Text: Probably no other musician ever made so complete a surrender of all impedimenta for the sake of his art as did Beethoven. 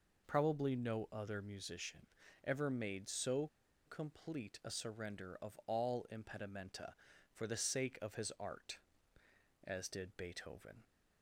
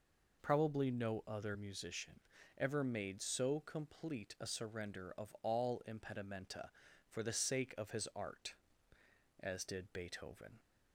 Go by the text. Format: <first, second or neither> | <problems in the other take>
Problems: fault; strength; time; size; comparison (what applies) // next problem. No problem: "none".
second | pauses between "musician" and "ever"; slight; at 2.0 s; 0.36 s long; slight in the second // pauses between "so" and "complete"; at 3.4 s; 0.39 s long